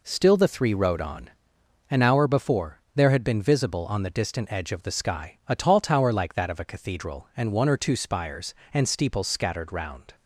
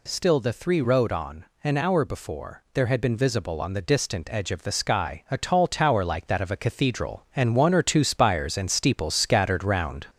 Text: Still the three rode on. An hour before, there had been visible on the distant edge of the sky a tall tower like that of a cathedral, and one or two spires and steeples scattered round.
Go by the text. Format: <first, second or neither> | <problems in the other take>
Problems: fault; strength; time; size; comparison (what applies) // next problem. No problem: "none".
first | gets louder; slight; throughout; 3.5 dB